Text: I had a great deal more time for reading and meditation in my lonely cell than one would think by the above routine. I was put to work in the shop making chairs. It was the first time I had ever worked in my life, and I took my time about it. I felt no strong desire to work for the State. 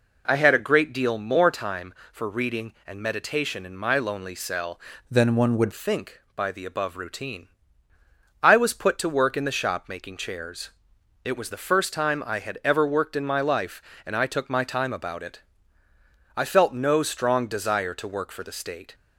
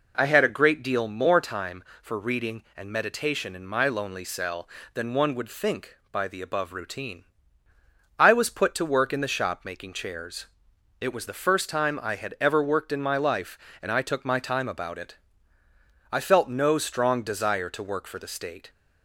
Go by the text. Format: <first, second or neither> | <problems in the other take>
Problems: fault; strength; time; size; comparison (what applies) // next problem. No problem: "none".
second | changes voice from "than" to "would"; from 5.0 to 5.7 s; 0.7 s long